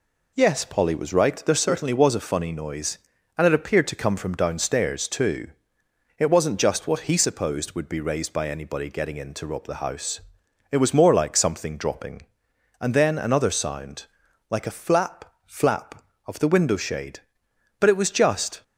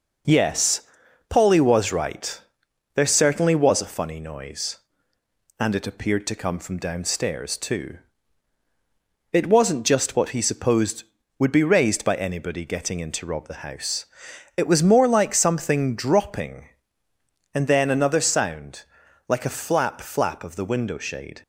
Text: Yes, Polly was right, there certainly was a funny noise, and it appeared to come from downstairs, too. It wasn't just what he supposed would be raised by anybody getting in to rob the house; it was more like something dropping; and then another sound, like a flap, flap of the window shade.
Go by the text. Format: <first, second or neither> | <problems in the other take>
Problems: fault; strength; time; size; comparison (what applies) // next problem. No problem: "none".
second | goes on to say "But it was just"; noticeable; from 17.7 s on; 0.84 s long